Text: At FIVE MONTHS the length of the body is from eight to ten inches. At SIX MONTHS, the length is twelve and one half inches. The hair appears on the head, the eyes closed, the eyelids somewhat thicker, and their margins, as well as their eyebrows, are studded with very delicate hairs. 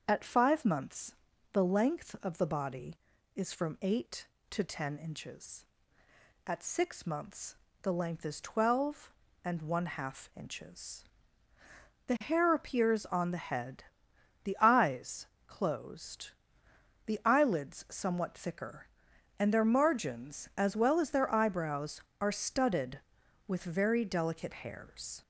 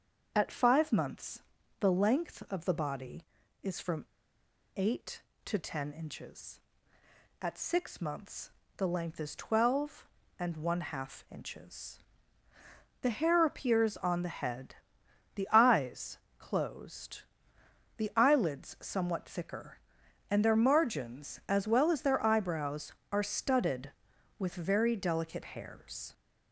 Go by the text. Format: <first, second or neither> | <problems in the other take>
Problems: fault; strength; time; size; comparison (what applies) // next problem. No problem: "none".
first | starts louder than the rest; until 1.3 s; 7 dB; also in the first // pauses between "MONTHS" and "the"; at 1.4 s; 0.38 s long; also in the first // pauses between "from" and "eight"; noticeable; at 4.0 s; 0.73 s long // pauses between "eyes" and "closed"; slight; at 16.1 s; 0.18 s long; slight in the first